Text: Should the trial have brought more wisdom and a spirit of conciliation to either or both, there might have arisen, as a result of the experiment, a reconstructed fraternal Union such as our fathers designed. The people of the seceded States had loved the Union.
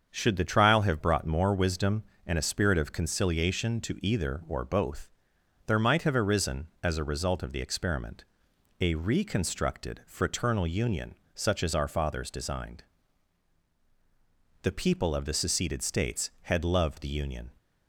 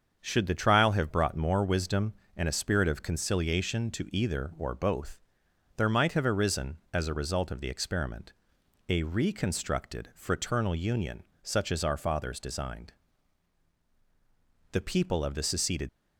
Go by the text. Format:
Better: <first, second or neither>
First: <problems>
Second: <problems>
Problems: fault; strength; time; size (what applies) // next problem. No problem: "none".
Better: first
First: starts louder than the rest; until 1.1 s; 7 dB // pauses between "Union" and "such"; slight; at 11.1 s; 0.20 s long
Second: starts louder than the rest; until 1.2 s; 7 dB // pauses between "Union" and "such"; slight; at 11.2 s; 0.20 s long // stops before "States had loved the Union"; at 15.8 s